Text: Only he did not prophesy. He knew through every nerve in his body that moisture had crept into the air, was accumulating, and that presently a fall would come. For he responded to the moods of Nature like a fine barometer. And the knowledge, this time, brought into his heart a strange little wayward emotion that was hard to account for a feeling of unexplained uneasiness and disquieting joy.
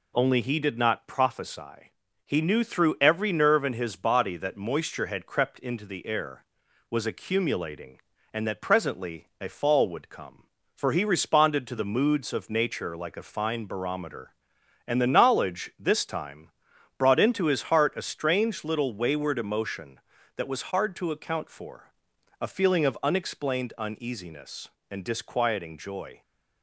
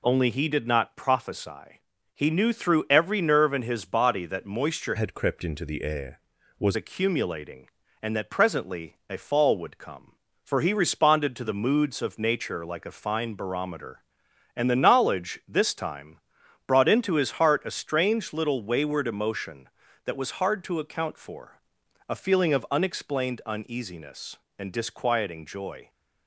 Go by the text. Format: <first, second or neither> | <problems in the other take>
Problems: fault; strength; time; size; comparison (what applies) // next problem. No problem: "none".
first | changes voice from "had" to "was"; from 4.9 to 6.7 s; 1.8 s long // pauses between "for" and "a"; noticeable; at 21.5 s; 0.50 s long; noticeable in the first